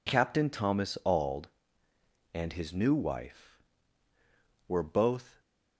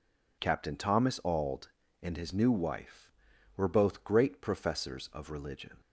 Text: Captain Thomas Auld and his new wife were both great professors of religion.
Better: second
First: stops before "great professors of religion"; at 5.4 s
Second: none

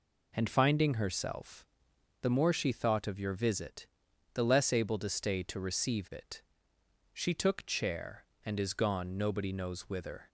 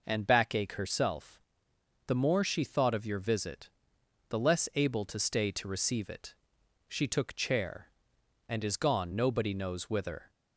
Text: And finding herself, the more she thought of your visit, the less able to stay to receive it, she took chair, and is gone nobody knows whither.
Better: first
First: none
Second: says "backache" for "finding"; at 0.2 s

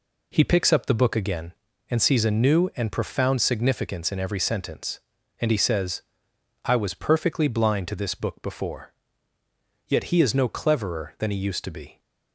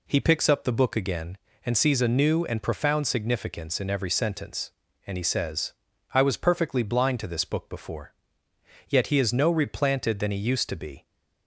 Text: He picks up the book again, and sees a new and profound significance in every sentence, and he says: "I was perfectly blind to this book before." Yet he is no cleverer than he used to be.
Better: first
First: none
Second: says "replanted" for "cleverer"; at 9.5 s

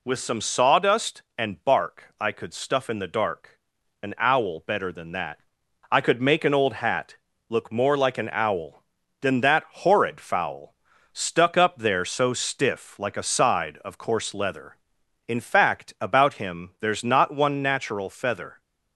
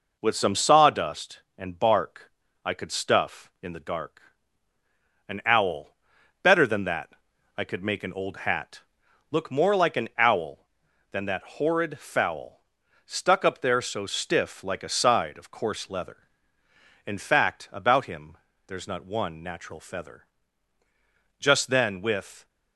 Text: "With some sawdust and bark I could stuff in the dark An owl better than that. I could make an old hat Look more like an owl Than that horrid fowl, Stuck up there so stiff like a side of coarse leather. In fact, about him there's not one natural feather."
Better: first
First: pauses between "dark" and "An"; at 3.6 s; 0.42 s long // pauses between "hat" and "Look"; slight; at 7.1 s; 0.34 s long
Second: pauses between "bark" and "I"; slight; at 2.3 s; 0.34 s long // pauses between "dark" and "An"; at 4.2 s; 1.0 s long // pauses between "owl" and "better"; noticeable; at 5.9 s; 0.46 s long // pauses between "hat" and "Look"; noticeable; at 8.8 s; 0.48 s long // pauses between "him" and "there's"; slight; at 18.3 s; 0.30 s long // goes on to say "Just then with"; noticeable; from 21.3 s on; 1.0 s long

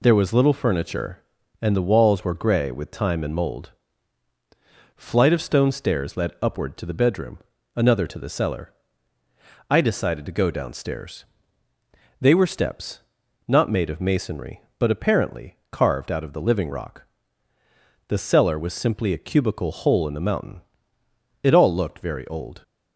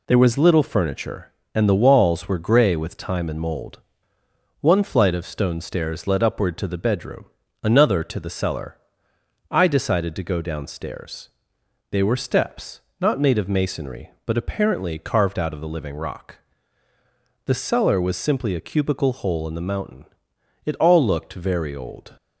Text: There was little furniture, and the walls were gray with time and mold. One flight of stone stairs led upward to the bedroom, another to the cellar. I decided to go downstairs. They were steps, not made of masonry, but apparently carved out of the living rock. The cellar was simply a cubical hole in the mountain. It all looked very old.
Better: second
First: skips "One"; at 4.3 s // pauses between "apparently" and "carved"; slight; at 15.5 s; 0.16 s long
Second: none

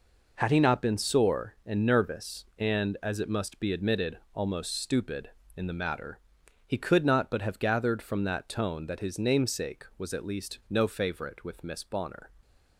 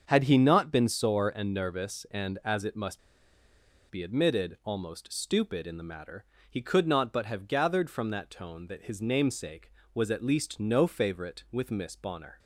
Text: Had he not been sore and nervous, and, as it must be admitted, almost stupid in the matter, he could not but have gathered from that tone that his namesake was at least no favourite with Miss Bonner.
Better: first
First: none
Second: starts louder than the rest; until 1.0 s; 7 dB // pauses between "must" and "be"; noticeable; at 2.9 s; 0.90 s long

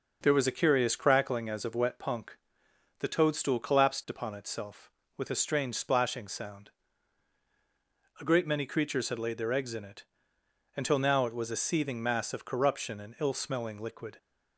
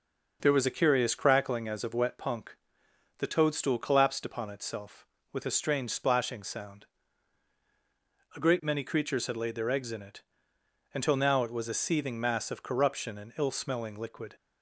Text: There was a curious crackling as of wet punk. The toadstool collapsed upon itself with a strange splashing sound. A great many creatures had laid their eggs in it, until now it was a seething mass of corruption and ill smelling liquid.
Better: neither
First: none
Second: none

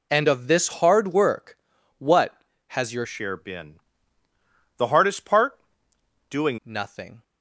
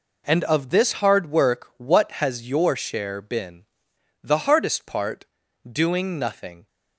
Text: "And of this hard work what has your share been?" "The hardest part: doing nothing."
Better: second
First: pauses between "work" and "what"; at 1.5 s; 0.40 s long // changes voice from "share" to "doing"; from 3.0 to 6.5 s; 3.5 s long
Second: none

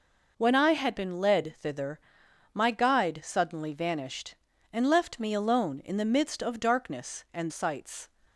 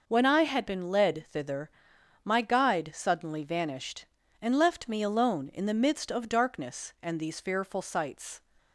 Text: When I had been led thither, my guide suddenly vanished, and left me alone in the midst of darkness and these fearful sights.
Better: second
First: skips "these fearful"; at 7.5 s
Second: none

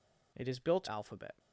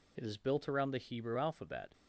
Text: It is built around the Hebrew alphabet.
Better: second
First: skips "around the Hebrew"; at 0.8 s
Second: none

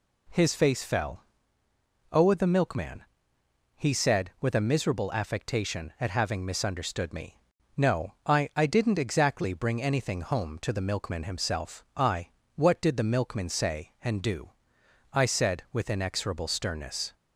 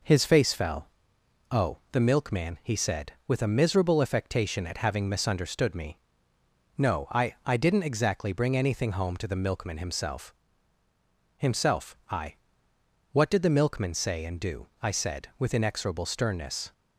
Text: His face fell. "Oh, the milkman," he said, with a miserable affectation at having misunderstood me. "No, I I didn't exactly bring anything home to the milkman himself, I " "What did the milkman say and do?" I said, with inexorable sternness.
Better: first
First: none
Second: says "himself" twice; at 11.3 s

